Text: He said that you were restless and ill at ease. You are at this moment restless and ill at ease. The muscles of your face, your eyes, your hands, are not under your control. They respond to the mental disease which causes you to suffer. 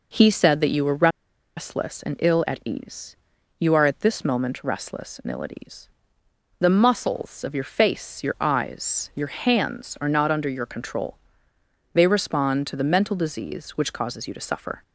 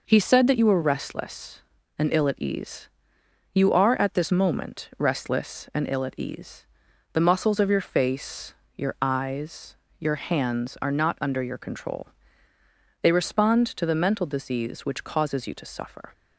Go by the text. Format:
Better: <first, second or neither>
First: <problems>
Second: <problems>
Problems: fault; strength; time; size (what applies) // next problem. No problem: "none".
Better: second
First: pauses between "were" and "restless"; noticeable; at 1.0 s; 0.48 s long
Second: none